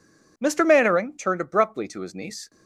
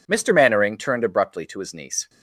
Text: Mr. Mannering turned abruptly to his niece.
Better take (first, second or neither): neither